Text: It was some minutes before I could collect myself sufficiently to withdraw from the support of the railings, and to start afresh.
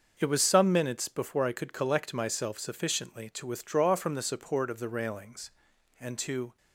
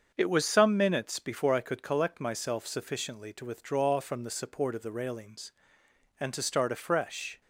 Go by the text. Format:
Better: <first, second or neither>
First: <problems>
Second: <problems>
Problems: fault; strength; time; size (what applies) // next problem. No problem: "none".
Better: second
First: starts louder than the rest; until 1.1 s; 6.5 dB // stops before "start afresh"; at 6.5 s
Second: starts louder than the rest; until 1.1 s; 7 dB